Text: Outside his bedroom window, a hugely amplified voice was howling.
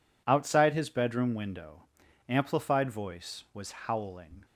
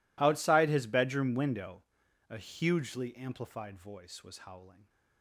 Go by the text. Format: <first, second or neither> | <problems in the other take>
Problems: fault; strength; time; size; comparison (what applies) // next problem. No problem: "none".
second | skips "a hugely"; at 2.0 s